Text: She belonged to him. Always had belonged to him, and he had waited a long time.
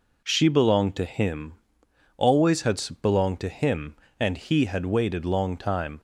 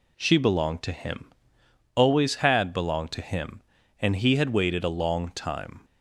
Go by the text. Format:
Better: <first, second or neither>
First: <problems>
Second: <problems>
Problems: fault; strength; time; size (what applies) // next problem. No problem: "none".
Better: second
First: pauses between "had" and "belonged"; slight; at 2.8 s; 0.20 s long // skips "a"; at 5.2 s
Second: none